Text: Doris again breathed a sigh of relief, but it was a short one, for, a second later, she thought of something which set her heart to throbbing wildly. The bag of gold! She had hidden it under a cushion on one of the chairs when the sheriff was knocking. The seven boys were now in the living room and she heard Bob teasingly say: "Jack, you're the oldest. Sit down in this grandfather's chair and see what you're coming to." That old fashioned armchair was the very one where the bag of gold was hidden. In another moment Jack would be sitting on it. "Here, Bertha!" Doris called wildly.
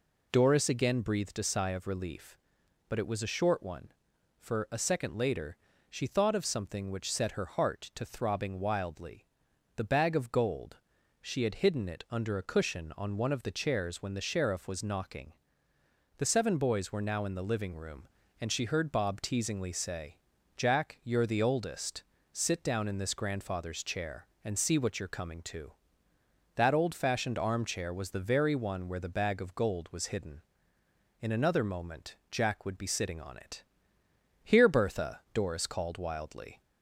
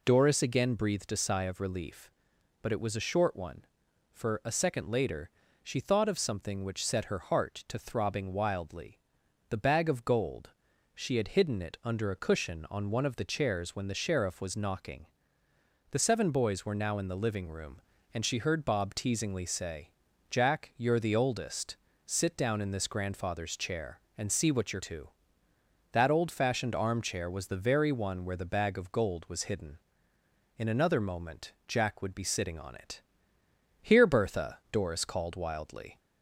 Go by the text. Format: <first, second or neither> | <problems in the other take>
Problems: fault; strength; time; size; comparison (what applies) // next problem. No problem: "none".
first | skips "coming"; at 24.8 s